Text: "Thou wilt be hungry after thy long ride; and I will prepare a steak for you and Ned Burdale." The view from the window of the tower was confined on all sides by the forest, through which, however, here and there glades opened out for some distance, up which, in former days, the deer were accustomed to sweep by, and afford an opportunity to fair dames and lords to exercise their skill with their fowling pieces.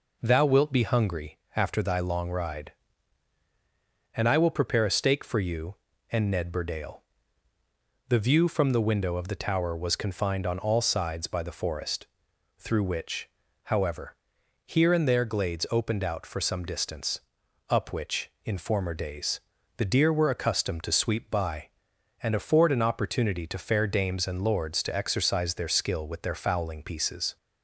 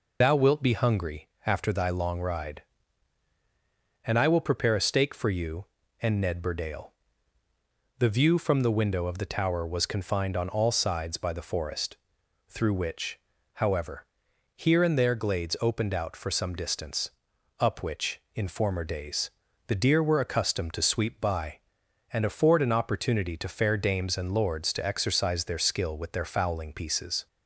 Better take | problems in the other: first | loses the start of "Thou"; at 0.2 s; 95 ms // pauses between "hungry" and "after"; slight; at 1.2 s; 0.16 s long; slight in the first

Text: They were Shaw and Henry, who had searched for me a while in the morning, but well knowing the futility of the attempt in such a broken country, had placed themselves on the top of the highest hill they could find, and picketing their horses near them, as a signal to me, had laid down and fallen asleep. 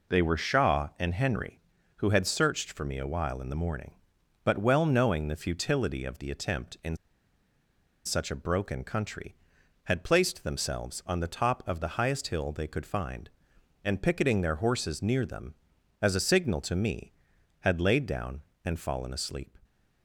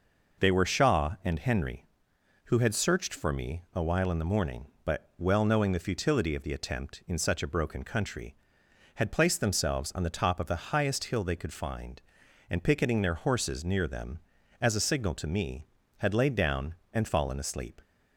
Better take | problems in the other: second | pauses between "in" and "such"; at 6.9 s; 1.0 s long

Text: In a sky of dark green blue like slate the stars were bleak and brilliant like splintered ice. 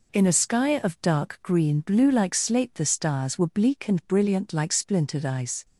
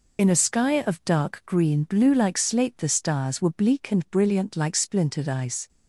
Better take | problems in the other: first | loses the start of "In"; at 0.1 s; 50 ms

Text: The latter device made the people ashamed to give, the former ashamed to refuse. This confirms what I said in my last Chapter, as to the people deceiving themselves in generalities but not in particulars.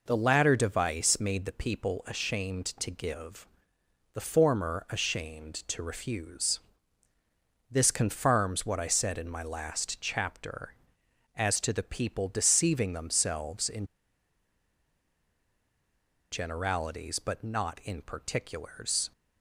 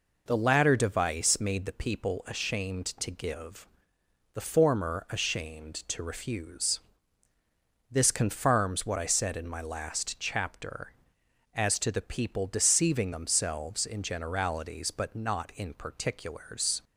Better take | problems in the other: second | pauses between "in" and "generalities"; strong; at 13.8 s; 2.4 s long

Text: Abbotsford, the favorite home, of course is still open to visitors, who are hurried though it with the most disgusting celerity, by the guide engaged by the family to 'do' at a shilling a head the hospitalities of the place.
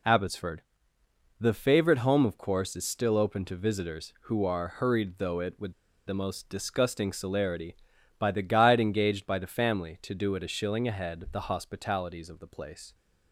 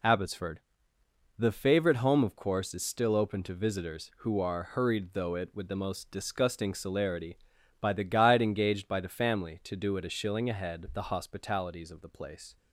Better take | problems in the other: second | pauses between "with" and "the"; slight; at 5.7 s; 0.34 s long

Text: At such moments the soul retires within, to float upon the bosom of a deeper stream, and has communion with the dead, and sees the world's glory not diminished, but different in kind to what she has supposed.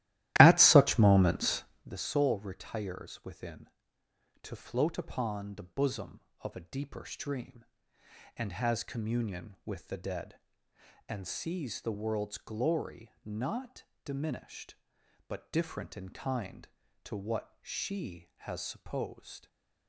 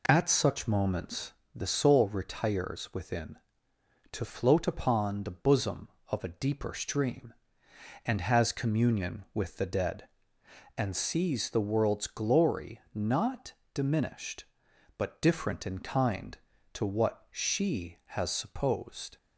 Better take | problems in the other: second | starts louder than the rest; strong; until 1.9 s; 15 dB // pauses between "moments" and "the"; slight; at 1.6 s; 0.20 s long; slight in the second // pauses between "not" and "diminished"; slight; at 13.8 s; 0.20 s long; slight in the second // stays silent after the last word; slight; from 19.3 s on; 0.5 s long

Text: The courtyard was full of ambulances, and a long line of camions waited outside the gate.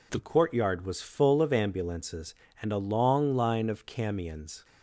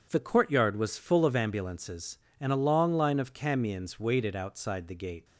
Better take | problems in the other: second | stops before "waited outside the gate"; at 4.6 s

